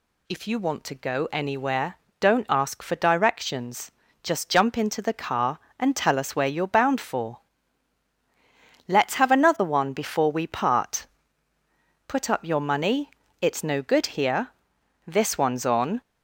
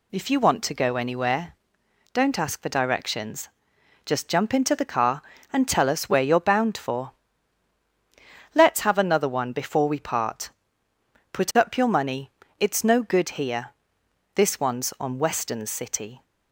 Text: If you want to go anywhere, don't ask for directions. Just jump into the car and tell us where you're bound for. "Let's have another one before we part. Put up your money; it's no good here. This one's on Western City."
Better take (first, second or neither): second